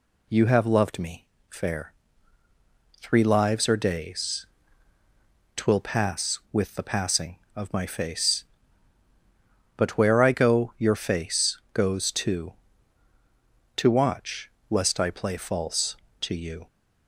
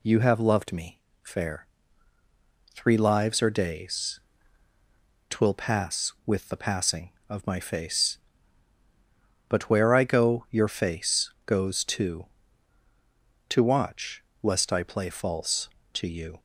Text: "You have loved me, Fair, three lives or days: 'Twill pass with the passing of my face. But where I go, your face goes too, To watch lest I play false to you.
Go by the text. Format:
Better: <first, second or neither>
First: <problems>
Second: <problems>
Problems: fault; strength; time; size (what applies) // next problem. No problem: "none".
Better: neither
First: pauses between "watch" and "lest"; slight; at 14.4 s; 0.22 s long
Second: pauses between "watch" and "lest"; slight; at 14.2 s; 0.22 s long